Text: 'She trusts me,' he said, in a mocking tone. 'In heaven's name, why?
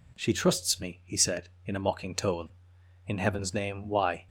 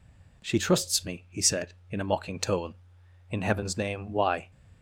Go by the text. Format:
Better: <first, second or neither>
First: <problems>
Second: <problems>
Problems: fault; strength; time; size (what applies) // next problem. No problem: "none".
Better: neither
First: none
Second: none